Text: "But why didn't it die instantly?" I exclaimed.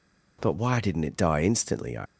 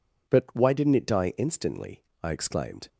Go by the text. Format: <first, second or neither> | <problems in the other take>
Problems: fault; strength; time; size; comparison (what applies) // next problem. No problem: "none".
second | stops before "exclaimed"; at 2.0 s